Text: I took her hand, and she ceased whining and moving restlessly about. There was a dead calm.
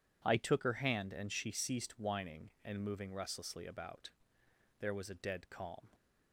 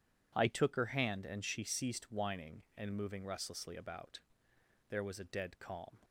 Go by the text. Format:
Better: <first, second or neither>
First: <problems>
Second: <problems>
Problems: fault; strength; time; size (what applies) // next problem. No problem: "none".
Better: neither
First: none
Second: none